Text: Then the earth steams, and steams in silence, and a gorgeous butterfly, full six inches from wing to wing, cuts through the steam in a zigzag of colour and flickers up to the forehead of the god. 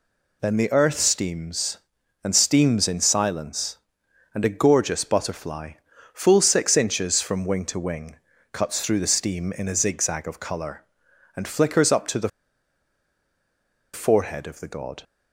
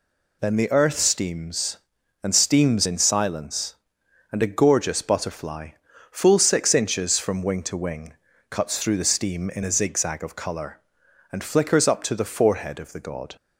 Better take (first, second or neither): second